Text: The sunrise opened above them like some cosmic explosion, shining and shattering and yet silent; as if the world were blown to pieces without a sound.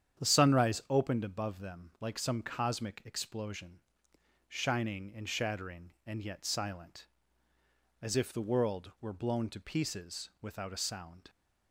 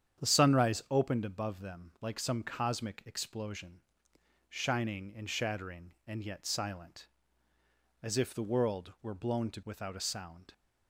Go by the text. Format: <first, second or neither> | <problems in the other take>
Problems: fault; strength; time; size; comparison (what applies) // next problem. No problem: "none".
first | starts louder than the rest; strong; until 1.2 s; 8.5 dB; strong in the first // skips "pieces"; at 9.6 s